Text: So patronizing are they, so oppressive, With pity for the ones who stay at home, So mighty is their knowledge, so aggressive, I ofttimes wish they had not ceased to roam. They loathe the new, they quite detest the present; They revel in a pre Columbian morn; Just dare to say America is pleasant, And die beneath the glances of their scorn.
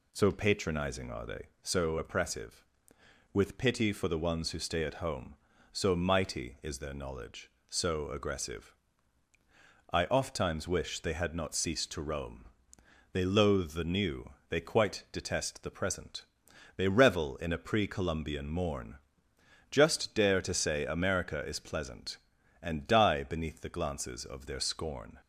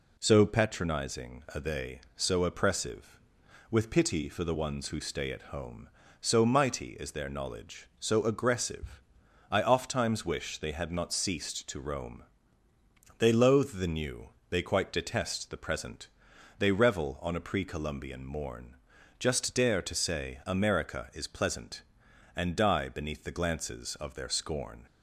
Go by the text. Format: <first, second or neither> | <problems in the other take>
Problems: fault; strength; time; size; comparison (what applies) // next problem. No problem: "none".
first | says "on" for "in"; at 17.2 s